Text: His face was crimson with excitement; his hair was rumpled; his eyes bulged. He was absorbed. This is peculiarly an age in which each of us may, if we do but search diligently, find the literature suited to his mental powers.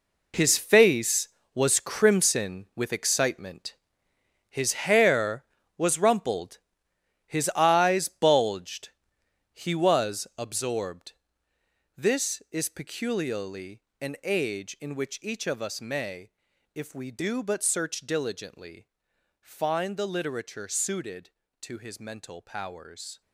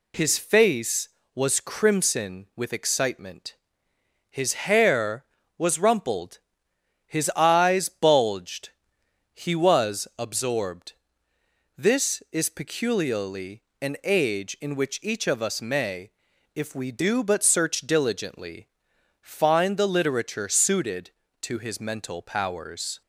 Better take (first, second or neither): second